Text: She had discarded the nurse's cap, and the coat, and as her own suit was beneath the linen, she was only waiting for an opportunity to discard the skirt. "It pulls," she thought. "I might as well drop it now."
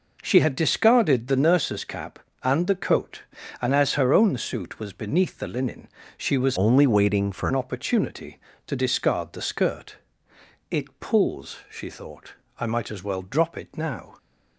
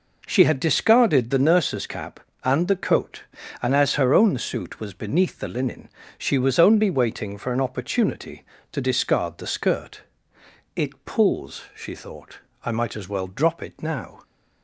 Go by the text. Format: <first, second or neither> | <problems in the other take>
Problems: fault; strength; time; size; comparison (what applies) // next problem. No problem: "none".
second | changes voice from "only" to "for"; from 6.5 to 7.4 s; 0.9 s long